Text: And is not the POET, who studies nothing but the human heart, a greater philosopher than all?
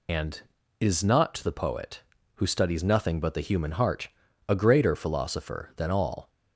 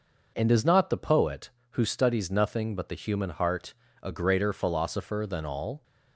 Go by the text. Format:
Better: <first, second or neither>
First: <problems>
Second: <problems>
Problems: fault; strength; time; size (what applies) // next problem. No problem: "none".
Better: second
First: loses the start of "And"; at 0.0 s; 70 ms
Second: none